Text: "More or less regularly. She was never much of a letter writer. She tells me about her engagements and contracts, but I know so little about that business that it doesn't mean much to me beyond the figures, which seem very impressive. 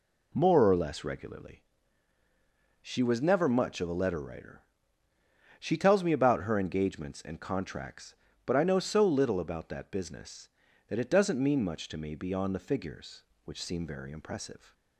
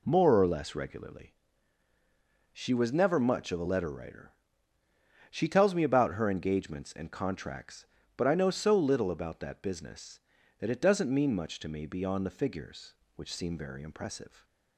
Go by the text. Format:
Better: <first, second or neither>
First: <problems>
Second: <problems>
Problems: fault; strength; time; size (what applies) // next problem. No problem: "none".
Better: neither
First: none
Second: none